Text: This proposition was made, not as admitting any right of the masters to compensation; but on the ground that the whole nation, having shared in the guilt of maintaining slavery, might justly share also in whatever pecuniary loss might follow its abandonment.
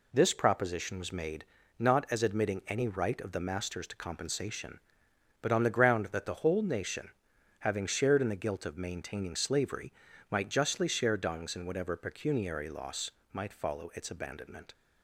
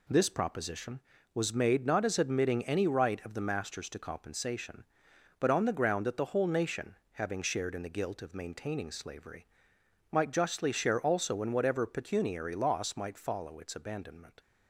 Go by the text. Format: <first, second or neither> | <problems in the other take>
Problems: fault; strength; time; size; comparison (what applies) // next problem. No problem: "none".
second | says "dungs" for "also"; at 11.1 s // pauses between "loss" and "might"; slight; at 13.1 s; 0.24 s long